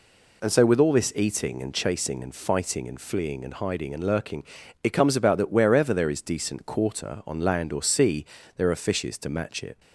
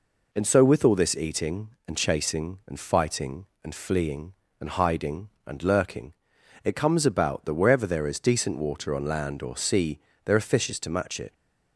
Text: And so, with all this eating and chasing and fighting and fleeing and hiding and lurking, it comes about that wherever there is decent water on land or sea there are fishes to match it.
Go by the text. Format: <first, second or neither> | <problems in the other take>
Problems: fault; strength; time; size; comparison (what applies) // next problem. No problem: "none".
second | says "quarter" for "water"; at 6.6 s // pauses between "sea" and "there"; slight; at 8.2 s; 0.32 s long; slight in the second